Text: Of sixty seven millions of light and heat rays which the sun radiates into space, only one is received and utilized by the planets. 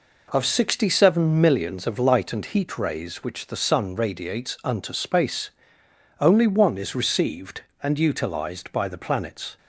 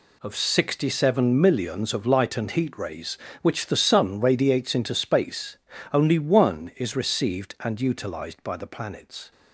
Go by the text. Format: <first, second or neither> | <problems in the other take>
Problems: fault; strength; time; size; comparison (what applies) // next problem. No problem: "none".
second | says "unto" for "into"; at 4.6 s